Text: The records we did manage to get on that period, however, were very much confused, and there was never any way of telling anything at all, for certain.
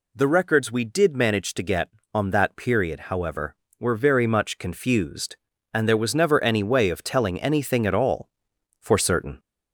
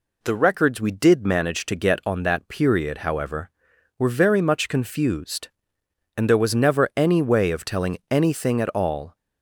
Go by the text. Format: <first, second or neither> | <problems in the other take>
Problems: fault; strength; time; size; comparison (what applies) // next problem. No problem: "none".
first | stops before "for certain"; at 9.1 s